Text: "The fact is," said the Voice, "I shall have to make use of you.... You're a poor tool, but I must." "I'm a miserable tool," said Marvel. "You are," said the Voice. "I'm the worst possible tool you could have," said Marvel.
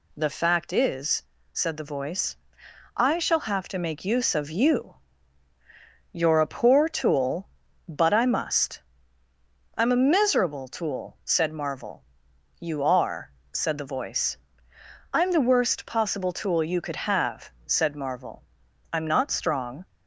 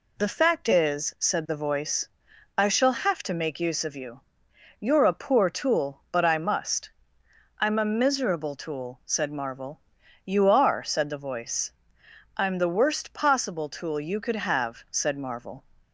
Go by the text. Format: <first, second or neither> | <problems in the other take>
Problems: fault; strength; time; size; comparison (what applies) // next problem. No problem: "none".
second | goes on to say "I'm not strong"; noticeable; from 18.9 s on; 0.94 s long